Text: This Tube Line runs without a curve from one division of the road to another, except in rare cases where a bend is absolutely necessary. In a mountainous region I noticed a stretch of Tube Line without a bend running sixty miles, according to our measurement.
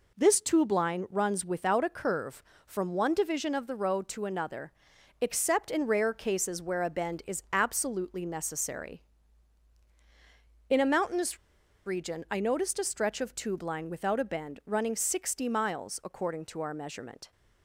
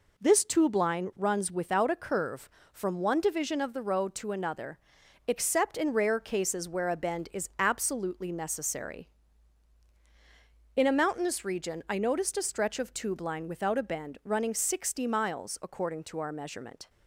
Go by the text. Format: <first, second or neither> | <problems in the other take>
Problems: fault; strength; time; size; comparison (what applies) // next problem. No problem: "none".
second | pauses between "mountainous" and "region"; noticeable; at 11.3 s; 0.49 s long